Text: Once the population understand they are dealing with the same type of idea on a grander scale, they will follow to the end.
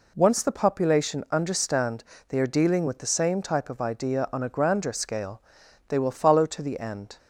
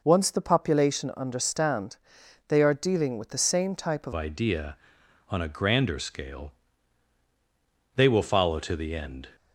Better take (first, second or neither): first